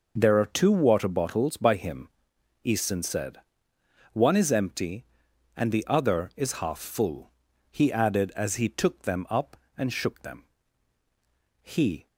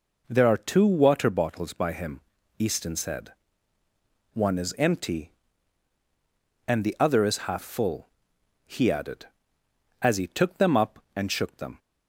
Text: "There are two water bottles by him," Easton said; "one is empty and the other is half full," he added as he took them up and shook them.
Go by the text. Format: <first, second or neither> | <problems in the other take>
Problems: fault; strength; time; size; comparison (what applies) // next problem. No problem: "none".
second | goes on to say "He"; slight; from 11.6 s on; 0.46 s long